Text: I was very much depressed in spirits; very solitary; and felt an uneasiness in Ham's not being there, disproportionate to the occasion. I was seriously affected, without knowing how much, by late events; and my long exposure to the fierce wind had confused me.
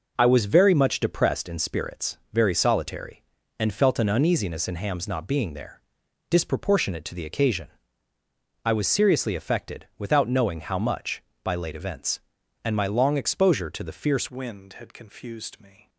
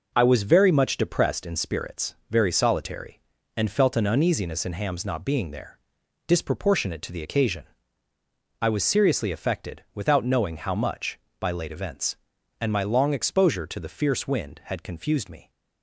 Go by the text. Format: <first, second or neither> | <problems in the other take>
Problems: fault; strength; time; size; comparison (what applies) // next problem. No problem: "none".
second | changes voice at "wind"; from 14.3 s on; 1.5 s long